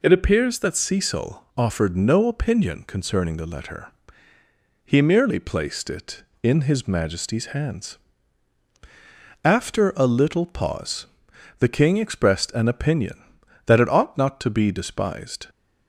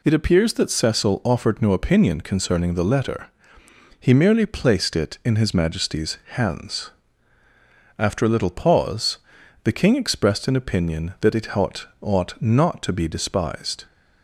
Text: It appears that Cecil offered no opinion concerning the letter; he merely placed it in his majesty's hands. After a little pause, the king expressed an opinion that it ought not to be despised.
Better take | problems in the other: first | says "ought" twice; at 12.0 s

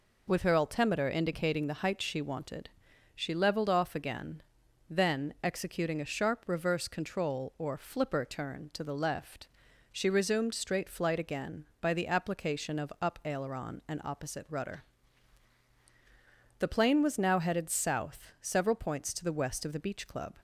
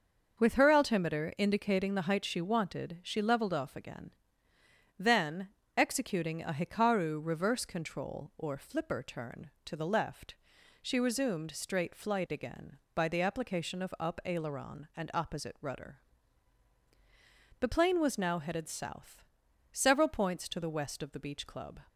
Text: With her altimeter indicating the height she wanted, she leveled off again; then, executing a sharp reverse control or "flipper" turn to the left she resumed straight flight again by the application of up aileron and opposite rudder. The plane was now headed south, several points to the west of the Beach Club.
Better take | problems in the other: first | starts louder than the rest; until 1.4 s; 6.5 dB // says "hikaru" for "sharp"; at 6.5 s // pauses between "left" and "she"; at 10.3 s; 0.44 s long; also in the first

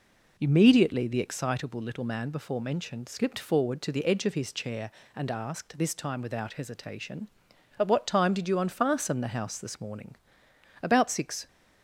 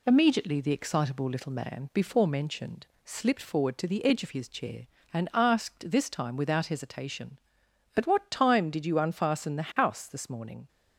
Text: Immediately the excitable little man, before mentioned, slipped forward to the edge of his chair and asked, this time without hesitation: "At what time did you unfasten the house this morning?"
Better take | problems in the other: second | goes on to say "About six"; noticeable; from 10.8 s on; 0.64 s long

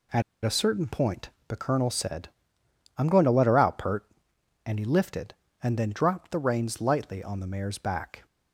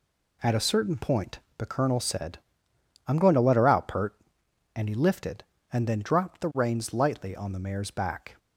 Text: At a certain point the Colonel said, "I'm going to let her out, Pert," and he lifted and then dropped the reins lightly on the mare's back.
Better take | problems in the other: second | pauses between "At" and "a"; slight; at 0.2 s; 0.22 s long // pauses between "point" and "the"; slight; at 1.2 s; 0.18 s long; slight in the second

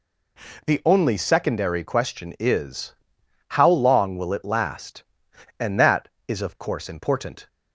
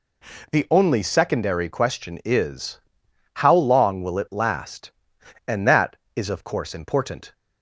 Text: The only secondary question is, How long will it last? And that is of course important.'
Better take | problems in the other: neither | none

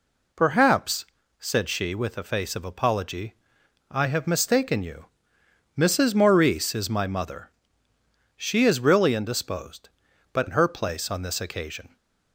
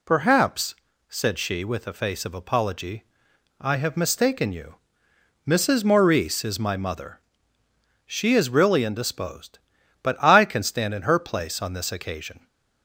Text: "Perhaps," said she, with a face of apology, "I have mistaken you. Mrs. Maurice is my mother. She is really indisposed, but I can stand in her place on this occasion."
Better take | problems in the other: second | skips "I can stand"; at 10.4 s

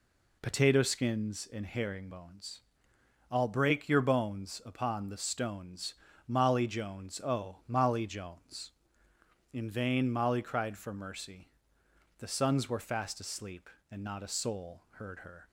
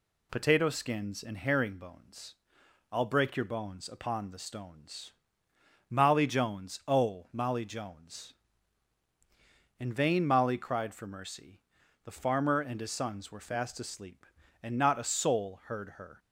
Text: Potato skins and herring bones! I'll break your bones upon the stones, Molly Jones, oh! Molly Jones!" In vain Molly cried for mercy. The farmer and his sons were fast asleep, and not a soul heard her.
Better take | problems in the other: second | skips "farmer and his"; at 12.2 s

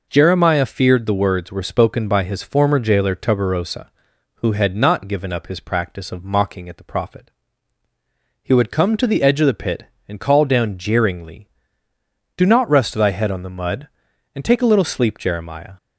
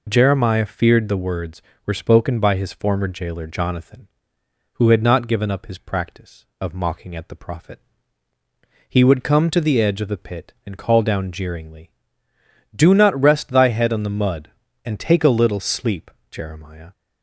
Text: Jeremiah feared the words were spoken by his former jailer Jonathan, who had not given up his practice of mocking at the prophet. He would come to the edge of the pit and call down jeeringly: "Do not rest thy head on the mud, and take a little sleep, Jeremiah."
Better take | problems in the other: second | says "Tuberosa" for "Jonathan"; at 3.1 s

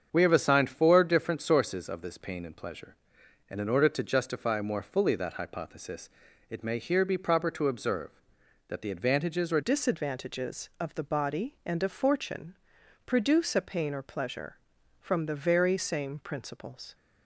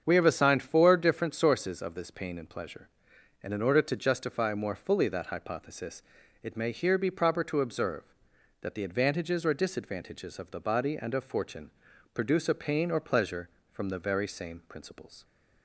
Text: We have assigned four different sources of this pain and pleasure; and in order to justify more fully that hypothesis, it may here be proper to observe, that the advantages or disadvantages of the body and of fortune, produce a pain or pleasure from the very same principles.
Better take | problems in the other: second | starts louder than the rest; strong; until 1.1 s; 7 dB; strong in the second // changes voice at "disadvantages"; from 9.6 s on; 7.3 s long

